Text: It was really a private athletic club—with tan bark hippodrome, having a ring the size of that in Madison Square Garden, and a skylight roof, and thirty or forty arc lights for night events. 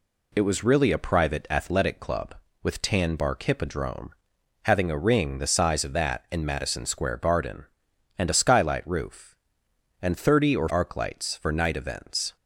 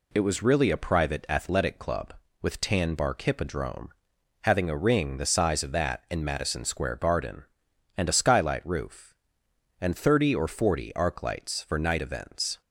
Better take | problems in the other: second | skips "forty"; at 10.6 s

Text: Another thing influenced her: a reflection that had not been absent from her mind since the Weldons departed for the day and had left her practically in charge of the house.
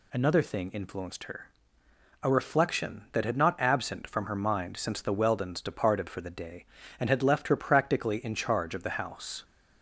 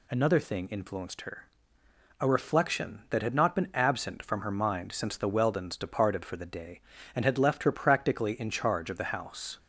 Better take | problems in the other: second | skips "been"; at 3.5 s

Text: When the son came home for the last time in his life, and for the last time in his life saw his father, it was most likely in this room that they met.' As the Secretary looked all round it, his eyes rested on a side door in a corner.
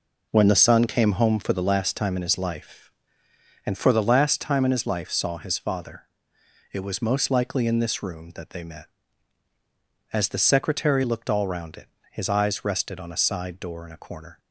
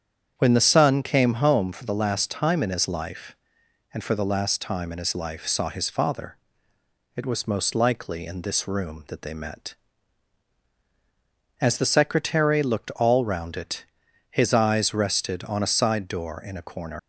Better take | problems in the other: first | starts louder than the rest; strong; until 1.3 s; 8 dB // leaves "corner" unfinished; at 16.9 s; 145 ms

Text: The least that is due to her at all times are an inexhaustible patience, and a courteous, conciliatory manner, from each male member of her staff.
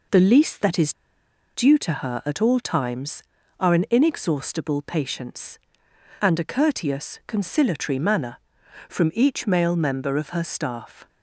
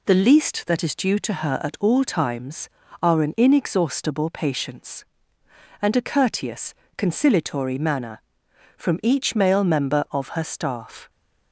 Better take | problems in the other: second | pauses between "is" and "due"; noticeable; at 0.9 s; 0.63 s long

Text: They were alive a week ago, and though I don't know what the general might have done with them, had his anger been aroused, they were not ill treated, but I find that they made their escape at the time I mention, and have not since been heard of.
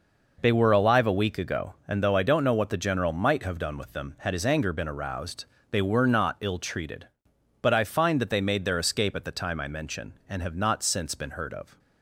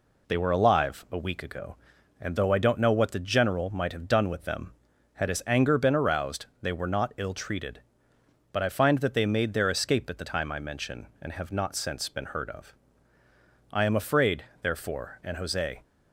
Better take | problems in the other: first | goes on to say "I am afraid therefore and Jose"; strong; from 13.7 s on; 2.1 s long

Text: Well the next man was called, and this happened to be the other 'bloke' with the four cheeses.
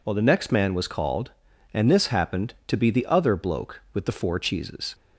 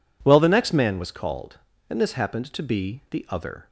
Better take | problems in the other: first | stops before "bloke with the four cheeses"; at 3.6 s

